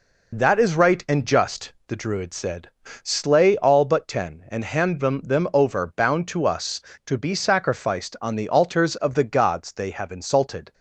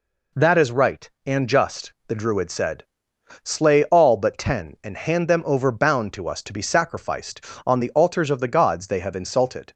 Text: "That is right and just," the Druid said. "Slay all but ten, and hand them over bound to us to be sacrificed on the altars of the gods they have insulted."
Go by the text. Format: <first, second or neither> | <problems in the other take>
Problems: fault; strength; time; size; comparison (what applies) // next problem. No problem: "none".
second | says "them" twice; at 5.2 s